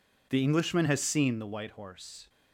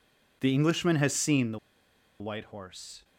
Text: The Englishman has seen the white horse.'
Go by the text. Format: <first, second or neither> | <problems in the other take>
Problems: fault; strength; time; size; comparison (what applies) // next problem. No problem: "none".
first | pauses between "the" and "white"; noticeable; at 1.5 s; 0.61 s long